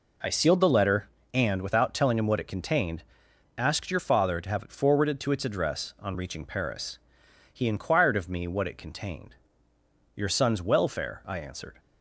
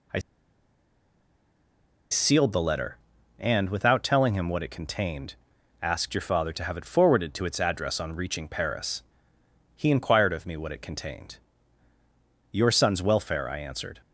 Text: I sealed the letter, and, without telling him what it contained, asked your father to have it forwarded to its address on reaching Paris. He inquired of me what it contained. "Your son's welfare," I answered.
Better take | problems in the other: first | pauses between "I" and "sealed"; strong; at 0.1 s; 1.9 s long

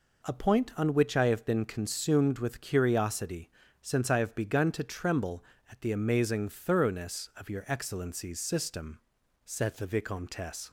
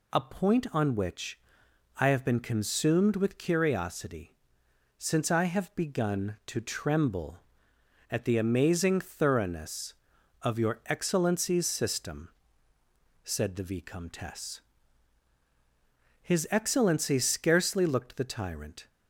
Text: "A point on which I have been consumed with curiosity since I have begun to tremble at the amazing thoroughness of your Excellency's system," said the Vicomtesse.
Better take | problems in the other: first | pauses between "which" and "I"; noticeable; at 1.3 s; 0.60 s long // pauses between "curiosity" and "since"; noticeable; at 4.3 s; 0.62 s long; slight in the first // goes on to say "His Excellency scarcely looked the tyrant"; strong; from 16.2 s on; 2.6 s long

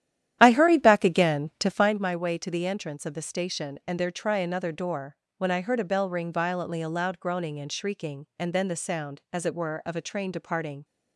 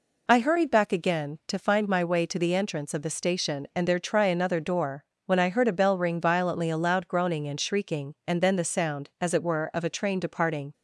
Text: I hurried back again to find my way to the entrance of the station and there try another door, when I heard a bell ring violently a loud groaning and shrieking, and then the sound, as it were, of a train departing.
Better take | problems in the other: second | starts louder than the rest; strong; until 2.0 s; 11 dB

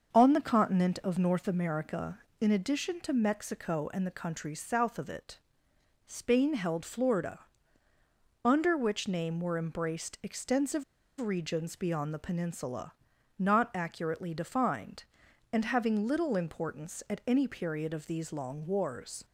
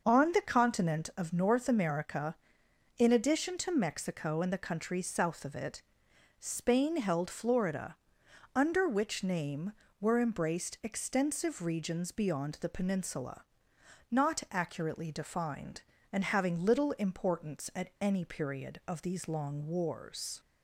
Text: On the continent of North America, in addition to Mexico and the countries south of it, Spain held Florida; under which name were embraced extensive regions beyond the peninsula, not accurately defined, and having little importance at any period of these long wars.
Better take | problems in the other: second | starts louder than the rest; until 1.1 s; 6.5 dB; noticeable in the second // pauses between "extensive" and "regions"; slight; at 10.8 s; 0.35 s long

